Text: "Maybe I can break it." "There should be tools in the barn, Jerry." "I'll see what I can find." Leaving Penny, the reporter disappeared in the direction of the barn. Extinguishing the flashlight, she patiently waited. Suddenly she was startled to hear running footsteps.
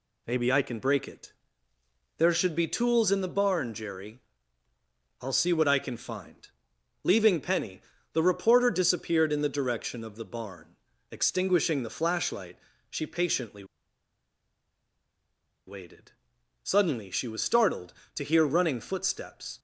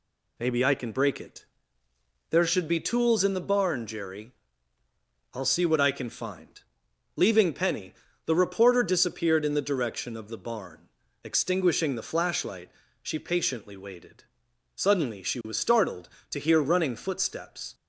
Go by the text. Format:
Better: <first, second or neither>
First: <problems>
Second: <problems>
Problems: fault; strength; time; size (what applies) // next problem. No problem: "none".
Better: second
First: pauses between "patiently" and "waited"; strong; at 13.6 s; 2.0 s long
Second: none